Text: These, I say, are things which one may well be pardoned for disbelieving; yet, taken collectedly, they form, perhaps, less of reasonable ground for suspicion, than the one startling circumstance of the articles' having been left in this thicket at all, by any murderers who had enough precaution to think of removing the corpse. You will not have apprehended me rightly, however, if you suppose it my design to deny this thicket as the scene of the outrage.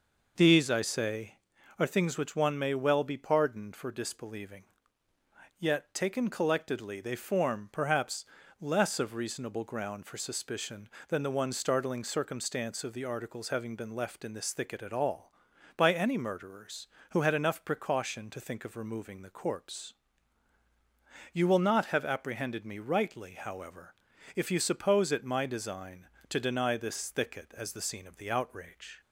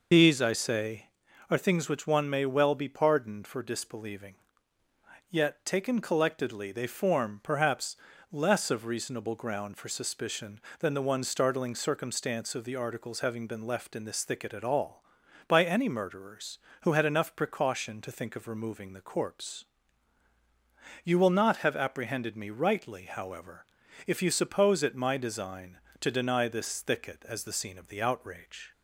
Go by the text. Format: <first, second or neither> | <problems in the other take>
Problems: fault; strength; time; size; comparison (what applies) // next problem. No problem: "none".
first | loses the start of "These"; at 0.1 s; 40 ms